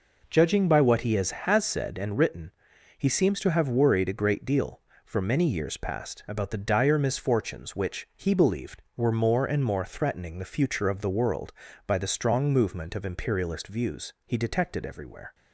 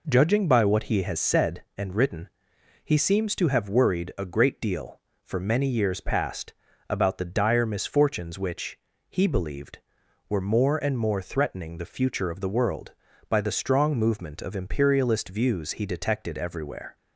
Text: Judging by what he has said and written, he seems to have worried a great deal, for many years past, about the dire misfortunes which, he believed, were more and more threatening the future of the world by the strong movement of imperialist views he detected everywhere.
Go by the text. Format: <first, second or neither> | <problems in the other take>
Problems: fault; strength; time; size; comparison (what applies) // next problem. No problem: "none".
second | says "has" twice; at 1.3 s